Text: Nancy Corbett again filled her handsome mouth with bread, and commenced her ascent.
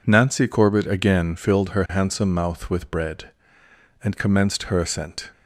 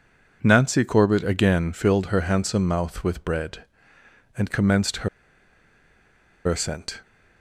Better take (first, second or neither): first